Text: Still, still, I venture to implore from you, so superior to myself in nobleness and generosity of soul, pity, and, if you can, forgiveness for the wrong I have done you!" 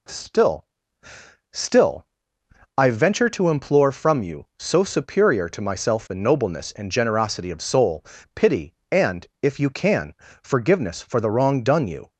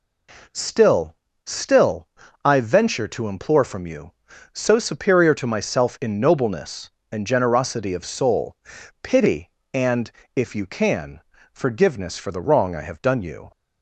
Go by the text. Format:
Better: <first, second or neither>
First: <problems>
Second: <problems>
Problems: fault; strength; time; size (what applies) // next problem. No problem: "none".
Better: second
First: skips "I have"; at 11.6 s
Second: none